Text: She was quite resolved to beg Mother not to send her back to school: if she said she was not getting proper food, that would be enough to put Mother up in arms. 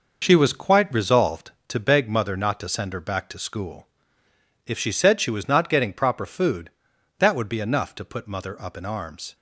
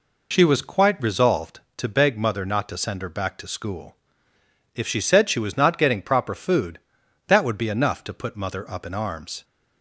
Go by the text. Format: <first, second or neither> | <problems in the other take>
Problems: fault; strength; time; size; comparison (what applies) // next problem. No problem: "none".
second | gets quieter; throughout; 6.5 dB